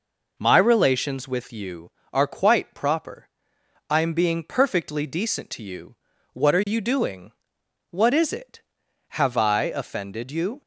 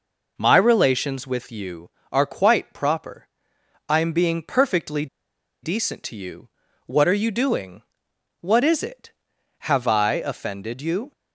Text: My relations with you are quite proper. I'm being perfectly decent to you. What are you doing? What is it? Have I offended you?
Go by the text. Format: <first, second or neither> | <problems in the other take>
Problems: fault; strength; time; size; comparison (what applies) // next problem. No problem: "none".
first | pauses between "perfectly" and "decent"; noticeable; at 5.0 s; 0.56 s long